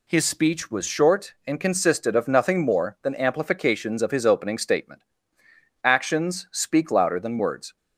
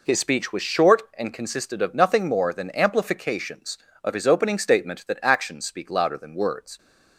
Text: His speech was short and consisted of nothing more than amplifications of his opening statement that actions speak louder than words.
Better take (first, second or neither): second